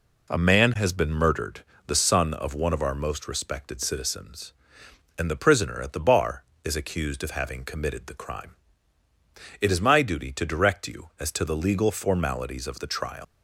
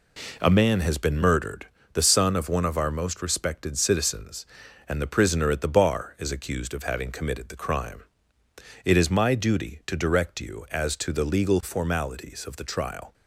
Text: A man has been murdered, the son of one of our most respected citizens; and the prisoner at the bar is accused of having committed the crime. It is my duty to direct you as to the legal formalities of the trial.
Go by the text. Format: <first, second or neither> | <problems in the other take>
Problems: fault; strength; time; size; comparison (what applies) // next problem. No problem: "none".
second | leaves "trial" unfinished; at 13.2 s; 150 ms